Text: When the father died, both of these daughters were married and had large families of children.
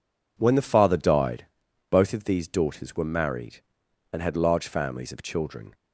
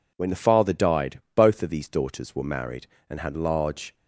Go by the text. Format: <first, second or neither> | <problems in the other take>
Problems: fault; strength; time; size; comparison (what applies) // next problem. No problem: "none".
first | stops before "families of children"; at 3.9 s